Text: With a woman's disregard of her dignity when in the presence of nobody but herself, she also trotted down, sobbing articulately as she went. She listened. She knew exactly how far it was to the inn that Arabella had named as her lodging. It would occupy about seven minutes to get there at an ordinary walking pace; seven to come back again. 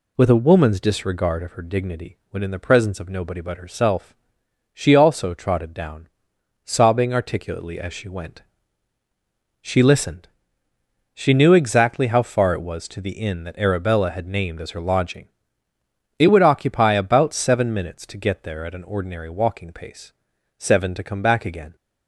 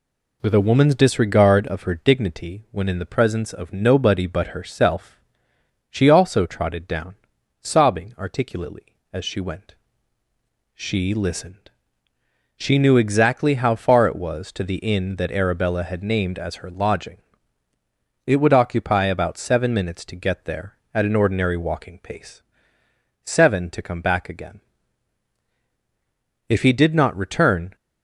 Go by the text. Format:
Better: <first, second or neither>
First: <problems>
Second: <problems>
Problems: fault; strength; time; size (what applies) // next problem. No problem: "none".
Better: first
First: none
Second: goes on to say "If he did not return"; noticeable; from 26.4 s on; 1.2 s long